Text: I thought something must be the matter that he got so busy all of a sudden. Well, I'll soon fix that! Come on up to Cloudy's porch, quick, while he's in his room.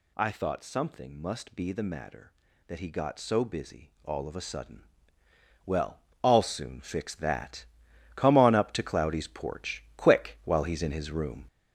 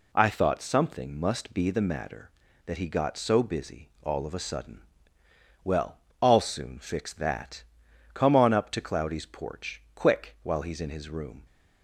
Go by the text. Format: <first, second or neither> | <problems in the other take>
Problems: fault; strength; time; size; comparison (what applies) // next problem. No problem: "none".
second | gets louder; throughout; 6 dB